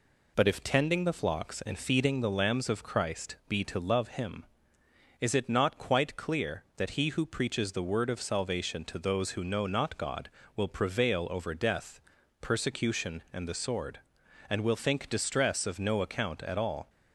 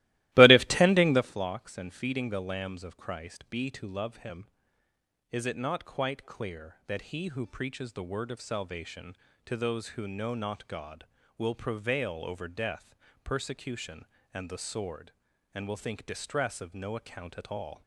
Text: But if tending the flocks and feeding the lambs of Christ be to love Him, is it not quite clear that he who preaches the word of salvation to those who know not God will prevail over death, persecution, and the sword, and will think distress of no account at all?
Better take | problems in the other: first | starts louder than the rest; strong; until 1.3 s; 17.5 dB

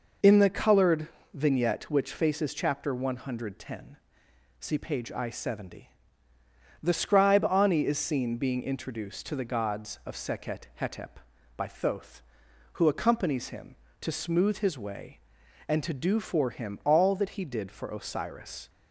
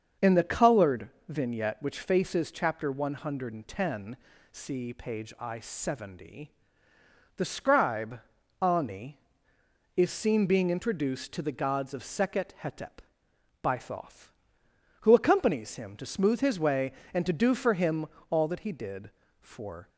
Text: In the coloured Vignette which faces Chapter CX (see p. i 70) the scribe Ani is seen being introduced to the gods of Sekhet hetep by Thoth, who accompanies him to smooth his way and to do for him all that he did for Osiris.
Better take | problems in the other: first | starts louder than the rest; until 1.3 s; 6.5 dB // pauses between "coloured" and "Vignette"; slight; at 1.1 s; 0.18 s long; slight in the first // pauses between "scribe" and "Ani"; at 8.1 s; 0.42 s long // pauses between "him" and "all"; slight; at 18.0 s; 0.24 s long // stops before "Osiris"; at 19.8 s

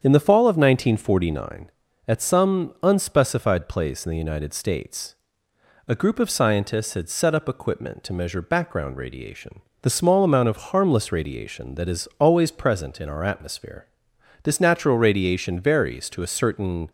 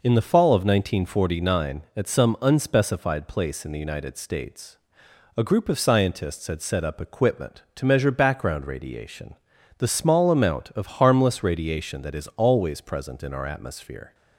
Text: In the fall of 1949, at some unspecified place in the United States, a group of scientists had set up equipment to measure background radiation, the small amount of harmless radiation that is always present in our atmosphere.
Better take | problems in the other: second | starts louder than the rest; strong; until 1.0 s; 7.5 dB // goes on to say "This natural radiation varies to a certain"; strong; from 14.4 s on; 2.4 s long

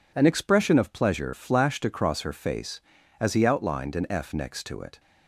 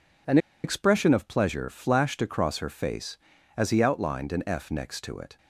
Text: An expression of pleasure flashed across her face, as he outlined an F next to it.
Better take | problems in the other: first | pauses between "An" and "expression"; slight; at 0.3 s; 0.26 s long

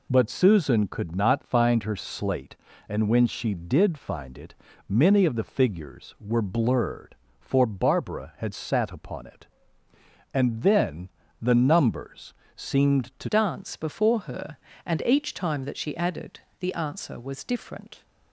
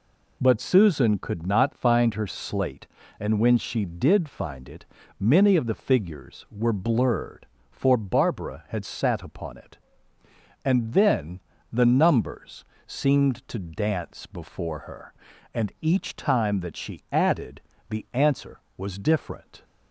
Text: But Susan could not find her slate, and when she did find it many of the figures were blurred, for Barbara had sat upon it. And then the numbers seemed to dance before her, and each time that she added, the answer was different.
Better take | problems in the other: second | pauses between "it" and "many"; slight; at 4.5 s; 0.34 s long; slight in the second // pauses between "then" and "the"; slight; at 11.0 s; 0.32 s long; slight in the second // pauses between "numbers" and "seemed"; slight; at 12.3 s; 0.22 s long; slight in the second // changes voice at "dance"; from 13.2 s on; 4.8 s long

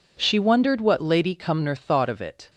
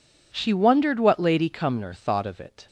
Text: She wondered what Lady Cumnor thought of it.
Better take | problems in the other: neither | none

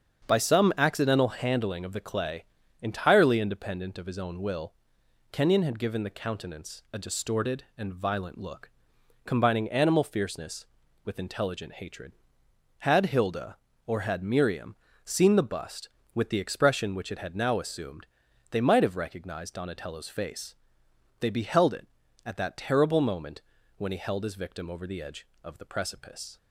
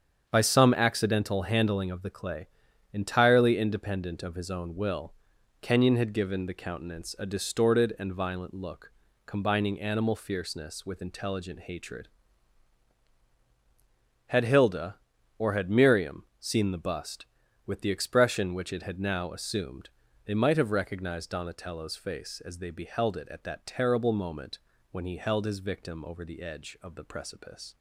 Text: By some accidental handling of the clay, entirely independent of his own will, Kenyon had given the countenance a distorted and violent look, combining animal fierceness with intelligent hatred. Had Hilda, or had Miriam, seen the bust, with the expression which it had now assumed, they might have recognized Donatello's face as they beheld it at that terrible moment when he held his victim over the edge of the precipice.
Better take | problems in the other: second | starts louder than the rest; strong; until 1.3 s; 7 dB; strong in the second // skips "as"; at 20.8 s // pauses between "moment" and "when"; slight; at 23.4 s; 0.36 s long; slight in the second

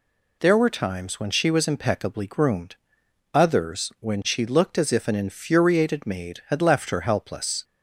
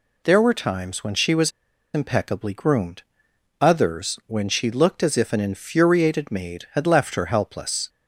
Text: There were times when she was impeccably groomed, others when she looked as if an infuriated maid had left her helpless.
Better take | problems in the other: first | pauses between "was" and "impeccably"; at 1.5 s; 0.43 s long

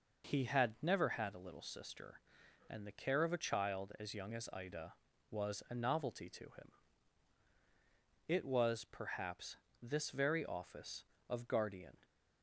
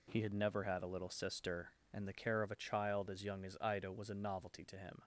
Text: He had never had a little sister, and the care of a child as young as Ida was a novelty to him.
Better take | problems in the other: second | goes on to say "It was perhaps this very office of guardian"; strong; from 8.2 s on; 3.7 s long

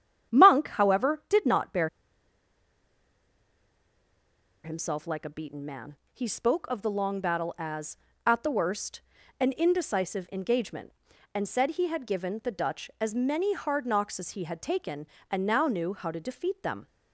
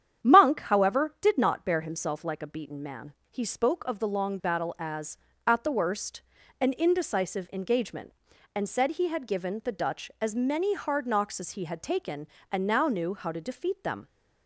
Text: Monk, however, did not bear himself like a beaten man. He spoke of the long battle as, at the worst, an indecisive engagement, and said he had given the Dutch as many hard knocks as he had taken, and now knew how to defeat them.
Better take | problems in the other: second | starts louder than the rest; strong; until 1.4 s; 9.5 dB; strong in the second // pauses between "bear" and "himself"; strong; at 1.8 s; 2.7 s long

